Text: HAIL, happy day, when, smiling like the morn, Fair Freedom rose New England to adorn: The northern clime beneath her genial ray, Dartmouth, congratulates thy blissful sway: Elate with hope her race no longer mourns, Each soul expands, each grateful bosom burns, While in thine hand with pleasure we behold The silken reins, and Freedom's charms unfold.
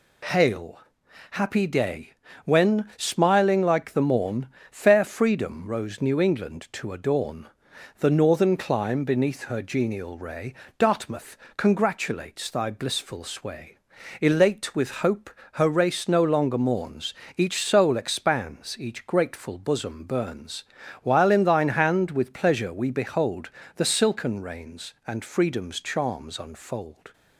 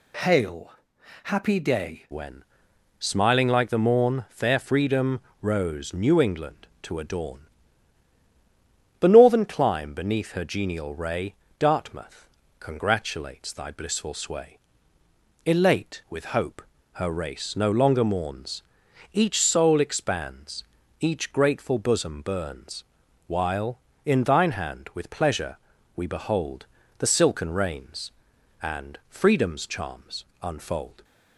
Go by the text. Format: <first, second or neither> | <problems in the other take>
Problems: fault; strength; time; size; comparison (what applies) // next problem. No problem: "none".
first | changes voice at "when"; from 2.1 s on; 28.9 s long // pauses between "Freedom" and "rose"; slight; at 5.1 s; 0.20 s long // pauses between "hope" and "her"; slight; at 16.6 s; 0.32 s long; slight in the first // pauses between "pleasure" and "we"; at 25.5 s; 0.40 s long // pauses between "behold" and "The"; slight; at 26.6 s; 0.32 s long; slight in the first // pauses between "charms" and "unfold"; slight; at 30.2 s; 0.18 s long